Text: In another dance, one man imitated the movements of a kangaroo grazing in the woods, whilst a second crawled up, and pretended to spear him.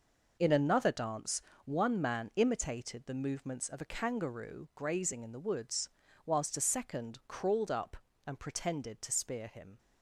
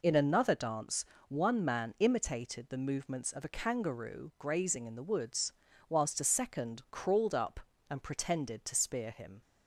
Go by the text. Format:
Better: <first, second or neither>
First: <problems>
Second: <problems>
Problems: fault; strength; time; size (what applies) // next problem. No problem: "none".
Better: second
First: gets quieter; strong; throughout; 9 dB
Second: none